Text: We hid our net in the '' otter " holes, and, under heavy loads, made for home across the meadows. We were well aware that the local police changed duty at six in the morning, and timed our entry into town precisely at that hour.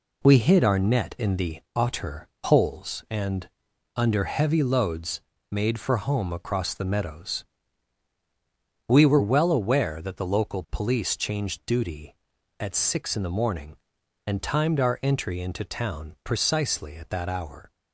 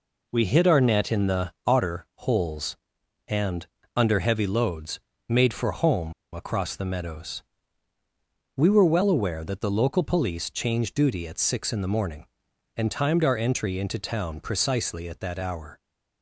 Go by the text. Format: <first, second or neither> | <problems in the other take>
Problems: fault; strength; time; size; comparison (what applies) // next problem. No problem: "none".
first | pauses between "home" and "across"; slight; at 6.1 s; 0.20 s long